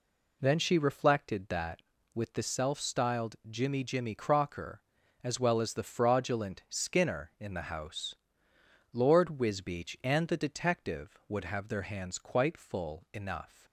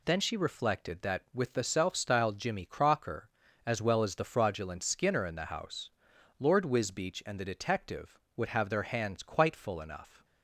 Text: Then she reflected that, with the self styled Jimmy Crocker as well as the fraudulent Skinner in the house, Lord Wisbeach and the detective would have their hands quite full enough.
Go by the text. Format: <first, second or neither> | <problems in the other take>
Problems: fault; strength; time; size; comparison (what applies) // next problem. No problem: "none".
second | says "Jimmy" twice; at 3.8 s